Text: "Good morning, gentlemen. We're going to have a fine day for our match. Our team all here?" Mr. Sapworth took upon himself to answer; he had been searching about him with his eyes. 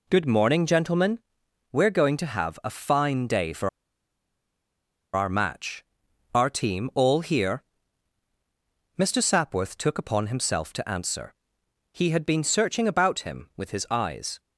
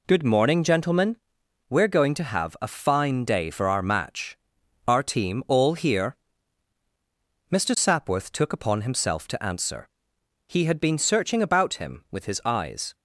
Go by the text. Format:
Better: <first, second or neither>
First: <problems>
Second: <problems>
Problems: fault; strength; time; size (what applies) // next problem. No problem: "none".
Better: second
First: pauses between "for" and "our"; strong; at 3.6 s; 1.4 s long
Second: none